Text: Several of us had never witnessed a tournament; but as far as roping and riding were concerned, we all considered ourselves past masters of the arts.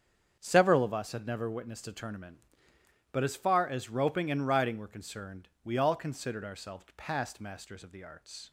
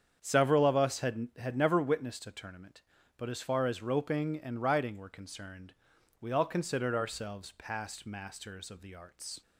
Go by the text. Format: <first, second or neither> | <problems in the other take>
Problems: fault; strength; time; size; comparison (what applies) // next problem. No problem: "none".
first | starts louder than the rest; strong; until 1.2 s; 8 dB; strong in the first // says "had" twice; at 1.3 s